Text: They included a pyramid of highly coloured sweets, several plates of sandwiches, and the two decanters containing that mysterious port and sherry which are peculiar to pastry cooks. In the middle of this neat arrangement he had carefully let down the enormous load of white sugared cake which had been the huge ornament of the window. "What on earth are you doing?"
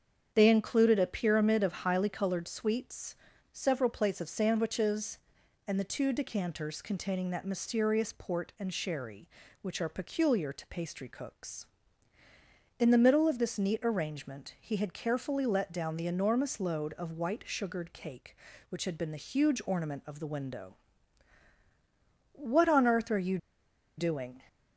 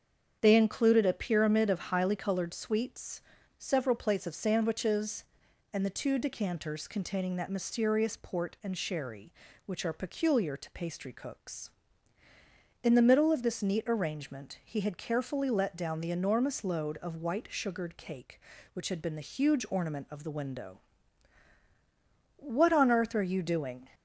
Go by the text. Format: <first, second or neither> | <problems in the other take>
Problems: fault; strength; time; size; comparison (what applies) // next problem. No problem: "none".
second | starts louder than the rest; strong; until 1.3 s; 7.5 dB; strong in the second // pauses between "you" and "doing"; noticeable; at 23.3 s; 0.59 s long